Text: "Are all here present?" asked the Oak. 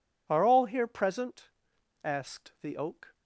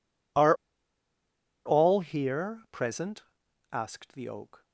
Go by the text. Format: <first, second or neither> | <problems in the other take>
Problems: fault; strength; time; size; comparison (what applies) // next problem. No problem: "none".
first | pauses between "Are" and "all"; at 0.5 s; 1.0 s long